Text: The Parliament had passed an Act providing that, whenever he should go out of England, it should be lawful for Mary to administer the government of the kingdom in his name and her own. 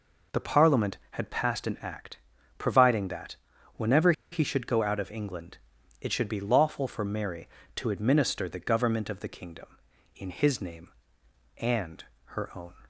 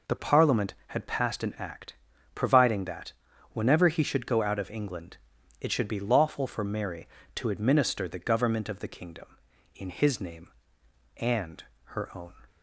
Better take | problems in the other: second | pauses between "Act" and "providing"; at 2.1 s; 0.40 s long; also in the second // pauses between "whenever" and "he"; slight; at 4.1 s; 0.20 s long // pauses between "and" and "her"; slight; at 12.0 s; 0.22 s long; slight in the second

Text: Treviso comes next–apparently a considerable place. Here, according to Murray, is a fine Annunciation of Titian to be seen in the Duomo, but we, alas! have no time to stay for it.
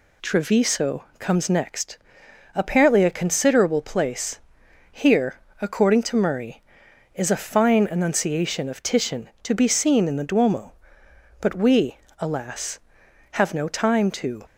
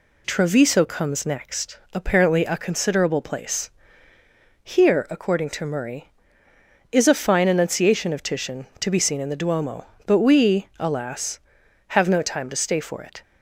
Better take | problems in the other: second | stops before "stay for it"; at 14.4 s

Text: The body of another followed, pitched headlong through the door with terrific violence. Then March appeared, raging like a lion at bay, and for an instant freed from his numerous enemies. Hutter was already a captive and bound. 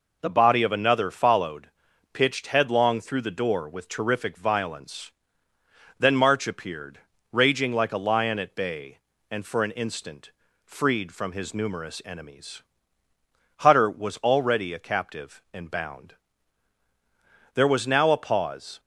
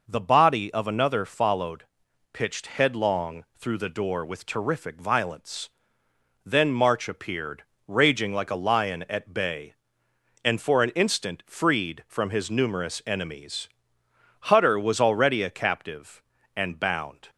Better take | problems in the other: second | pauses between "instant" and "freed"; slight; at 10.3 s; 0.32 s long // goes on to say "There was now a pause"; noticeable; from 17.5 s on; 1.2 s long

